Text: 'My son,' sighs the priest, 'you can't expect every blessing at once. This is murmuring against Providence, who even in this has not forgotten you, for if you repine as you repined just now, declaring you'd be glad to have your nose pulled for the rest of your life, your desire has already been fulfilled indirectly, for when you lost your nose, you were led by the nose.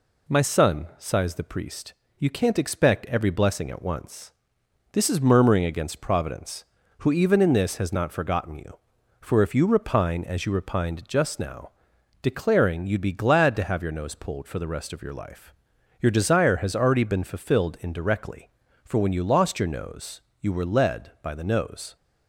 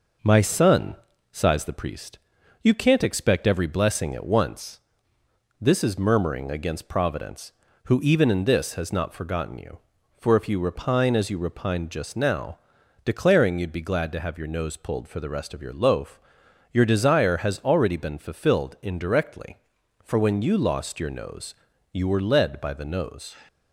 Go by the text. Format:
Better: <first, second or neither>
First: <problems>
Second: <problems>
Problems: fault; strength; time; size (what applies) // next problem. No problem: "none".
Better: first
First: none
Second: says "loaf" for "life"; at 15.7 s